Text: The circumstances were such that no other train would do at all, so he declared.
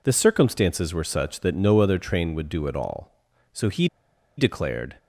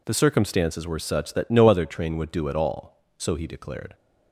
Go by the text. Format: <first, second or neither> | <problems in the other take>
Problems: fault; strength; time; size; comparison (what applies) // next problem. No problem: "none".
second | pauses between "he" and "declared"; noticeable; at 3.8 s; 0.51 s long